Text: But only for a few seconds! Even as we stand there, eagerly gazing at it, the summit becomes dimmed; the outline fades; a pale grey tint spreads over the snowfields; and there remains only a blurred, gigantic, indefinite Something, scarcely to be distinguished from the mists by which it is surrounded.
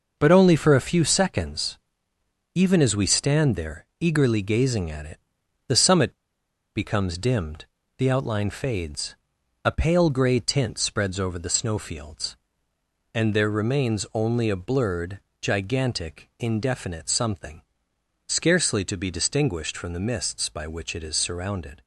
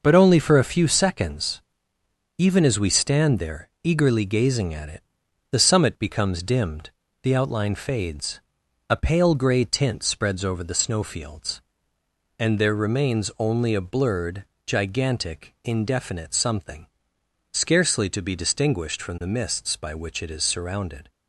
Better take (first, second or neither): second